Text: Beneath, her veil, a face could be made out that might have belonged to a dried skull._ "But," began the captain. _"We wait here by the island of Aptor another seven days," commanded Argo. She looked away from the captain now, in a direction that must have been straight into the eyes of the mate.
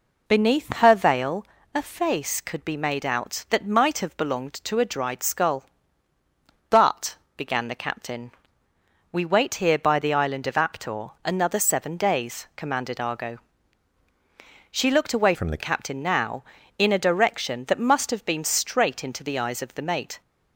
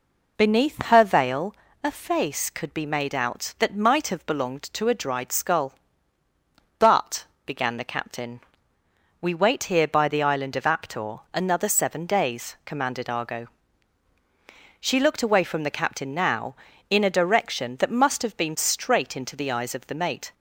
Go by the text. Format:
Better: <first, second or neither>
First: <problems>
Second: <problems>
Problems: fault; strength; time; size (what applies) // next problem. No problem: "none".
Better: second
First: changes voice from "from" to "the"; from 15.3 to 15.6 s; 0.3 s long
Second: none